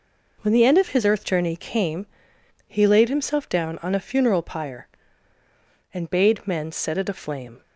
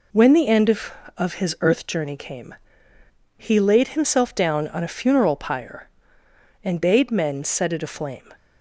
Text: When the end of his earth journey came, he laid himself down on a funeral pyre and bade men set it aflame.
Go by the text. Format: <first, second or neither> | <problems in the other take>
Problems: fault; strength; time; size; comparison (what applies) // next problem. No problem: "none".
first | says "of" twice; at 1.1 s